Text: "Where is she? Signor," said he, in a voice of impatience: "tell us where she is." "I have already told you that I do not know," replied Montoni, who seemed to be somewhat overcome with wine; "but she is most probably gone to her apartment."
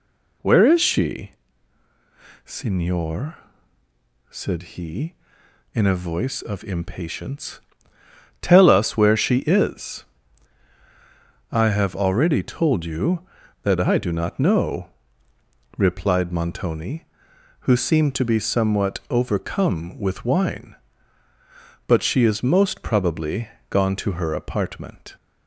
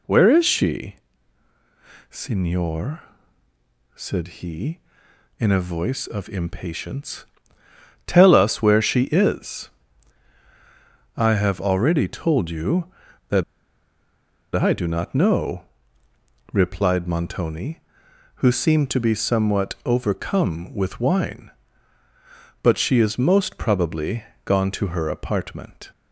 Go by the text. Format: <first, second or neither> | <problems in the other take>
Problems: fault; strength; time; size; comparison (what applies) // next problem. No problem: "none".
first | pauses between "that" and "I"; at 13.4 s; 1.1 s long // pauses between "probably" and "gone"; slight; at 24.2 s; 0.22 s long; slight in the first